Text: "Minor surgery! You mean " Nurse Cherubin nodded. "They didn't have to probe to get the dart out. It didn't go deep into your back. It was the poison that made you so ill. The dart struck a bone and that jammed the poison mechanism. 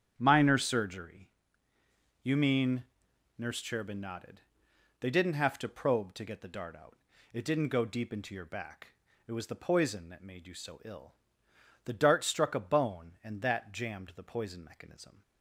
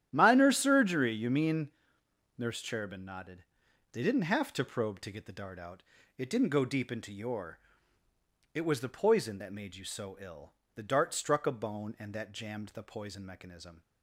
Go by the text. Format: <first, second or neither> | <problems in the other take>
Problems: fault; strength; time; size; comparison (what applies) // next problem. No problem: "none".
first | starts louder than the rest; strong; until 1.1 s; 10.5 dB; strong in the first // skips "back"; at 8.0 s